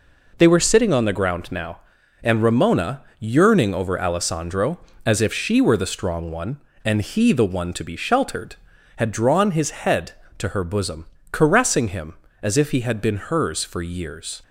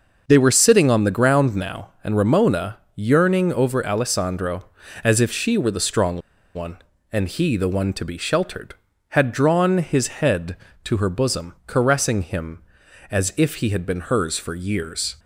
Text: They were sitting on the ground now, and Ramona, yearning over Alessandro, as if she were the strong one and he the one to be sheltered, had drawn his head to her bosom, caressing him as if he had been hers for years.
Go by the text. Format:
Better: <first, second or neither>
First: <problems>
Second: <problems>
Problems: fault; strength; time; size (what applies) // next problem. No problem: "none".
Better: first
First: none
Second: starts louder than the rest; noticeable; until 1.2 s; 6 dB // pauses between "strong" and "one"; slight; at 6.2 s; 0.35 s long